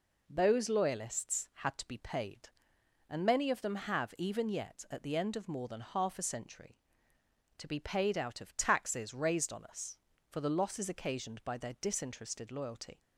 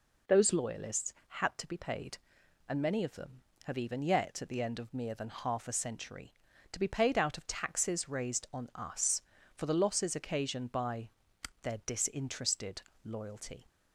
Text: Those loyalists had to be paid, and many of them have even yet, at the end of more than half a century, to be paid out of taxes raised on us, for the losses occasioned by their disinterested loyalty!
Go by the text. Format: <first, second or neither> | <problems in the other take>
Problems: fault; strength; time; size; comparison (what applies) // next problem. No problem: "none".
first | says "mere" for "more"; at 4.9 s // pauses between "by" and "their"; noticeable; at 11.0 s; 0.52 s long // pauses between "disinterested" and "loyalty"; slight; at 12.8 s; 0.22 s long